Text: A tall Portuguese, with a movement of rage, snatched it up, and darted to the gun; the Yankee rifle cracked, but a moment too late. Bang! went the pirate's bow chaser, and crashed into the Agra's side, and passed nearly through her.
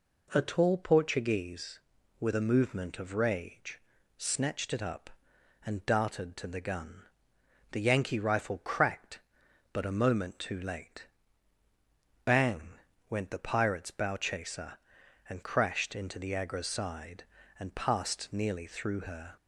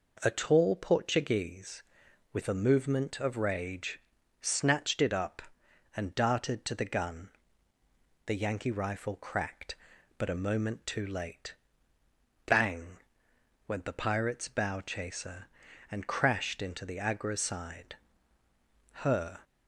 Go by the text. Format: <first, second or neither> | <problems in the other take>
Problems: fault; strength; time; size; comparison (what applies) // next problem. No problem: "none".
first | skips "and passed nearly through"; at 18.4 s